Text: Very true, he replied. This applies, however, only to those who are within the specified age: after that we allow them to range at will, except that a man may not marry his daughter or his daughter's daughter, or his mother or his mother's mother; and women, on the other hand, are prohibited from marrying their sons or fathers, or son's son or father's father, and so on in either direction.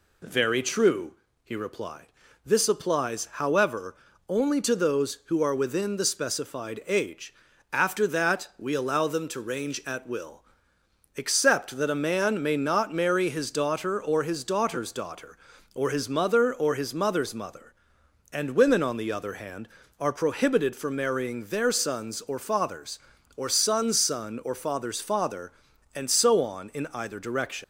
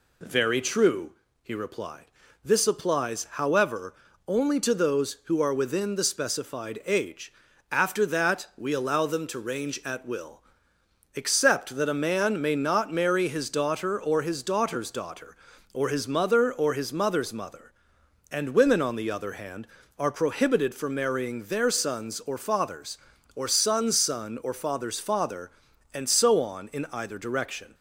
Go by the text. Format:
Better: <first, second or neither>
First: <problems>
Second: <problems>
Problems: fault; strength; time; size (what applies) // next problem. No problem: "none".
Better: second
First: leaves "direction" unfinished; at 27.6 s; 105 ms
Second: none